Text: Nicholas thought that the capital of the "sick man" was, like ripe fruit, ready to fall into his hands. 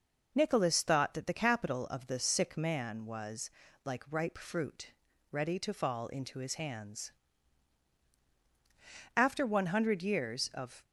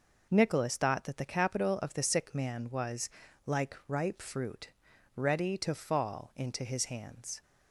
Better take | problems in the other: second | goes on to say "After one hundred years of"; strong; from 9.1 s on; 1.6 s long

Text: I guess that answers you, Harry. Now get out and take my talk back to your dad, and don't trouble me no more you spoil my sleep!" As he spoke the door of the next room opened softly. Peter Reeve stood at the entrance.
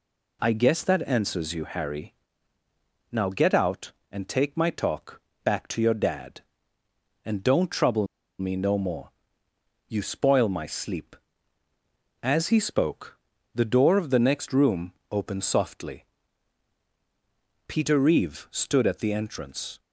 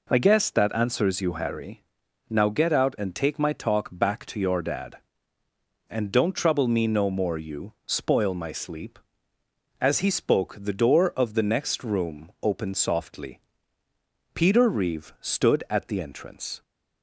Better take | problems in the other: second | pauses between "talk" and "back"; slight; at 5.2 s; 0.24 s long // pauses between "trouble" and "me"; slight; at 8.0 s; 0.33 s long // pauses between "more" and "you"; noticeable; at 9.0 s; 0.80 s long // pauses between "spoke" and "the"; slight; at 13.1 s; 0.34 s long // pauses between "room" and "opened"; slight; at 14.9 s; 0.18 s long

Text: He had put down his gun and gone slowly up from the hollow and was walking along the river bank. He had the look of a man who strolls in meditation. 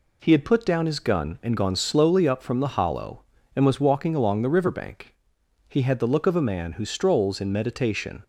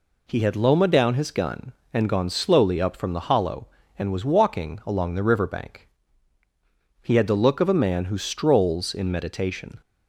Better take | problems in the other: first | says "loma" for "put"; at 0.5 s

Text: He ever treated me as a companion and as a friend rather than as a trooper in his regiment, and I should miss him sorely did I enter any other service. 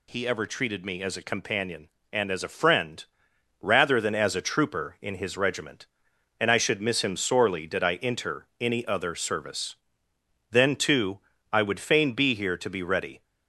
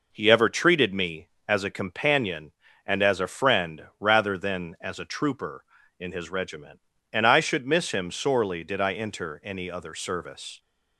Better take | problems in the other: second | pauses between "friend" and "rather"; noticeable; at 3.0 s; 0.56 s long // goes on to say "Then too I would fain be here to be ready"; strong; from 10.4 s on; 2.7 s long

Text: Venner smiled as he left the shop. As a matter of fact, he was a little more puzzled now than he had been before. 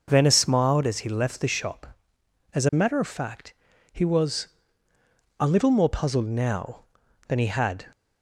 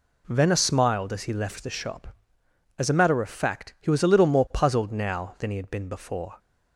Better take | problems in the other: second | pauses between "was" and "a"; noticeable; at 4.4 s; 0.92 s long // stops before "been before"; at 7.9 s

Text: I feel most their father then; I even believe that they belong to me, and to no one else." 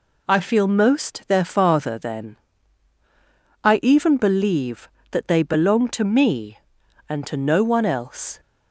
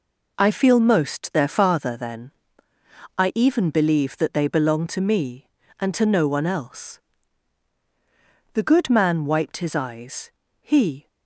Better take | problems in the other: first | goes on to say "The good man wiped his eyes he"; strong; from 8.5 s on; 2.5 s long

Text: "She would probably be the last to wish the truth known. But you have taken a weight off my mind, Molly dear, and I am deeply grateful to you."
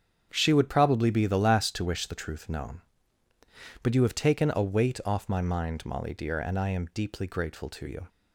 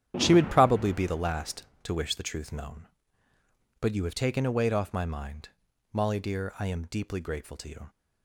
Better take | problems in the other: first | starts louder than the rest; strong; until 1.1 s; 10.5 dB; strong in the first // skips "and"; at 6.5 s

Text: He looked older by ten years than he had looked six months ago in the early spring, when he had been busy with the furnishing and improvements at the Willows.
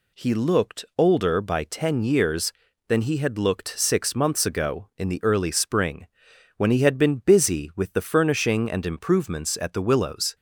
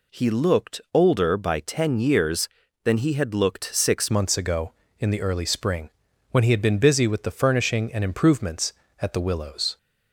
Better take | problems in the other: first | changes voice at "months"; from 4.1 s on; 5.6 s long

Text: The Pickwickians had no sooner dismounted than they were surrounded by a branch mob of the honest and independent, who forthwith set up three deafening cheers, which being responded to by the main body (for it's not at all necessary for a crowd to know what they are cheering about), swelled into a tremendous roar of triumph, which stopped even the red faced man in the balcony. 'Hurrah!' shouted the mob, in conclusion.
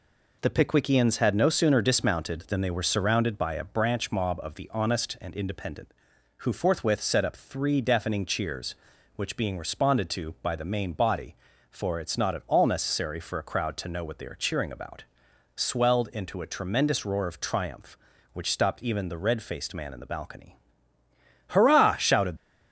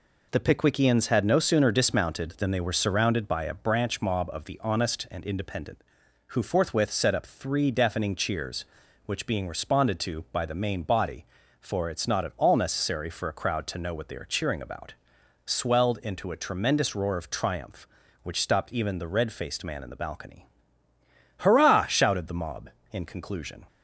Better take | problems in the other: second | stops before "the mob in conclusion"; at 22.3 s

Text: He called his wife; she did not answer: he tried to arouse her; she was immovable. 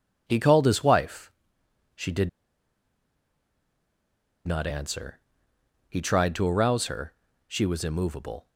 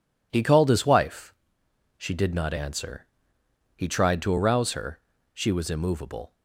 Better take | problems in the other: second | pauses between "did" and "not"; strong; at 2.2 s; 2.1 s long

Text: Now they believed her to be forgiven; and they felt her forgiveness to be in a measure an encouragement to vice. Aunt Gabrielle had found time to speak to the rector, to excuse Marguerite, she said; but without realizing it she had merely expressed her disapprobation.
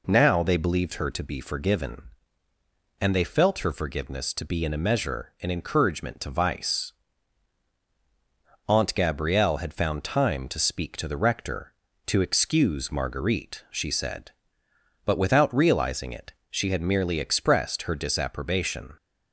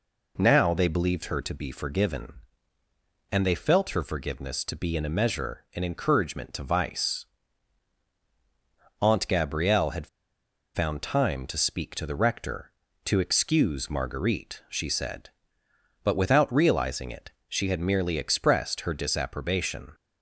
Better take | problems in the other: first | pauses between "had" and "found"; noticeable; at 10.0 s; 0.68 s long // pauses between "it" and "she"; slight; at 17.3 s; 0.18 s long; slight in the first

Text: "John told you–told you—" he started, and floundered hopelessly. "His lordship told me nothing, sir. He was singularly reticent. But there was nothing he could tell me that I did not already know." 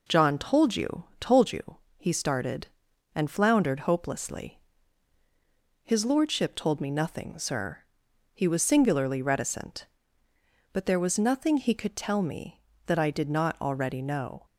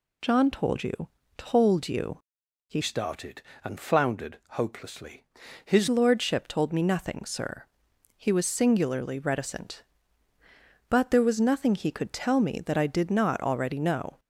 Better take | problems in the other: first | changes voice from "started" to "His"; from 2.8 to 5.8 s; 3.0 s long

